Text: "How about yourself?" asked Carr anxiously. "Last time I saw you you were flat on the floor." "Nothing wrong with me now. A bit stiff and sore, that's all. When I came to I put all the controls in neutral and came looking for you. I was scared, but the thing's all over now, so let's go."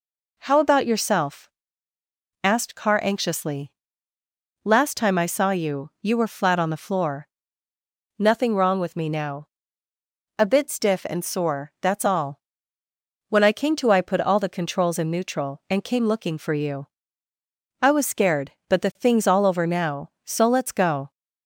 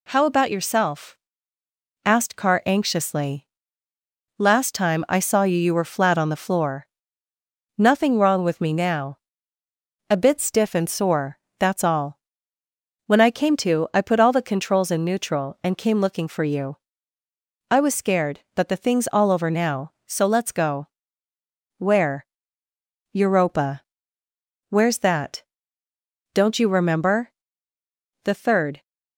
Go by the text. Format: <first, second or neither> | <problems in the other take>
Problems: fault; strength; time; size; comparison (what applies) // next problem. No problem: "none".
first | goes on to say "Where Europa Where's that Don't you remember The third"; strong; from 21.7 s on; 7.0 s long